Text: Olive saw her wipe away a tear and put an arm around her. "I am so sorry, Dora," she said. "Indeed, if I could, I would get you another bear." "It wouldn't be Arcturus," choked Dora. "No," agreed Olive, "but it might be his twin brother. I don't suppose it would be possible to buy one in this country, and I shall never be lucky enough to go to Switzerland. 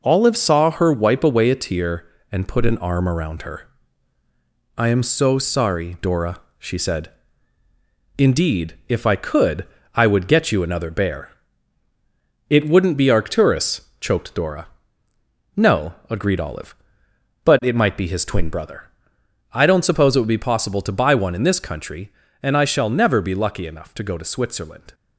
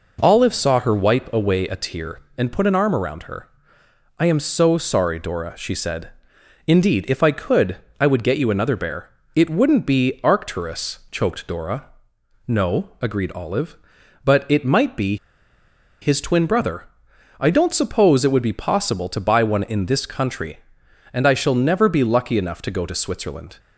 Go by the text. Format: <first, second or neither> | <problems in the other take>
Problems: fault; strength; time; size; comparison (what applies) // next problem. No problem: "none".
first | pauses between "be" and "his"; noticeable; at 15.1 s; 0.86 s long